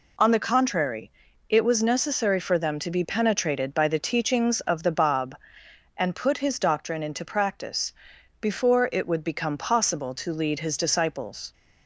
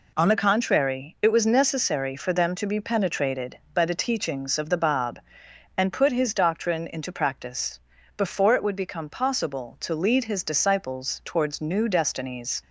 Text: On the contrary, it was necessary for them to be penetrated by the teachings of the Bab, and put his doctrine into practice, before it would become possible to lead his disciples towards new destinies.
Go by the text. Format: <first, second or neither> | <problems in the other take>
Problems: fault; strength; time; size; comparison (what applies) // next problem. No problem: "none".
second | stops before "towards new destinies"; at 11.5 s